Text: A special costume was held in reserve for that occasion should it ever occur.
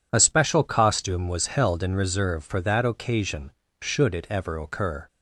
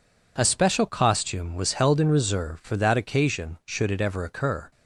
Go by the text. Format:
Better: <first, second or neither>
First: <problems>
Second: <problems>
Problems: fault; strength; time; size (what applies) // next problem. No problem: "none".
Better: neither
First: none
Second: none